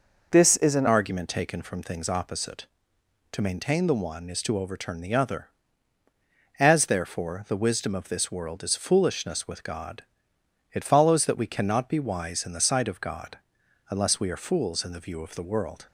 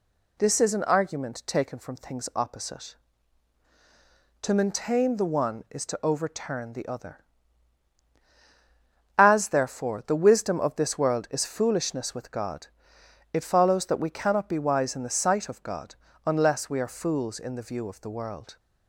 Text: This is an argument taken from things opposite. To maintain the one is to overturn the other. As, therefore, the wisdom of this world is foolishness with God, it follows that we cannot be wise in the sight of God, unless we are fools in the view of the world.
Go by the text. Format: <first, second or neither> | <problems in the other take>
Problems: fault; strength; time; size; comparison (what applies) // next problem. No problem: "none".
second | changes voice at "argument"; from 0.8 s on; 15.0 s long